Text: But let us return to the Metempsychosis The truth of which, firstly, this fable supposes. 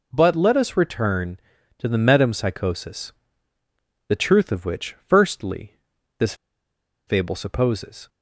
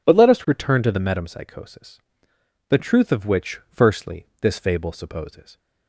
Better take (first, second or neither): second